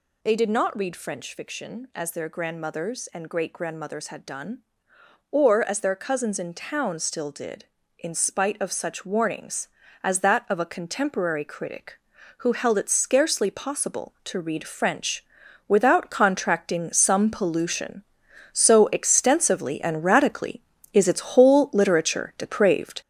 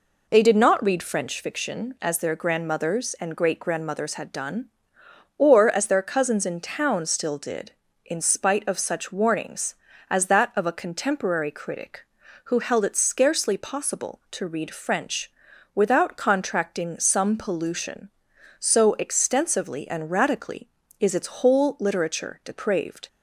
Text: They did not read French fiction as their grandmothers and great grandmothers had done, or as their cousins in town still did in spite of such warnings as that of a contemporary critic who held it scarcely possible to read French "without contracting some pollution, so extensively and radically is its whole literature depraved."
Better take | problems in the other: second | gets louder; throughout; 6.5 dB // pauses between "French" and "without"; at 15.2 s; 0.42 s long; also in the second

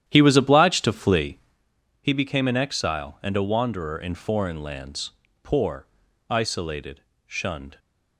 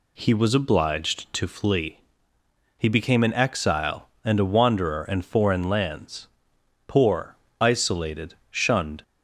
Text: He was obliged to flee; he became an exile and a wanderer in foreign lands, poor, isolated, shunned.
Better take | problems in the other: second | starts louder than the rest; strong; until 1.7 s; 11 dB

